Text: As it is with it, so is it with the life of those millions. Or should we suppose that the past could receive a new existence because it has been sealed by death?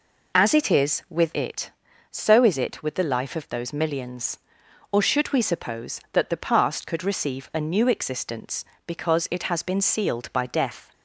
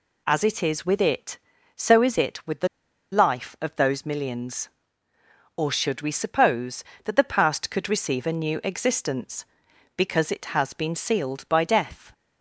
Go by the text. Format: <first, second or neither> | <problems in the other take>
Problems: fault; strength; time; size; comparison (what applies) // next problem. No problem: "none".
first | pauses between "the" and "life"; at 2.6 s; 0.44 s long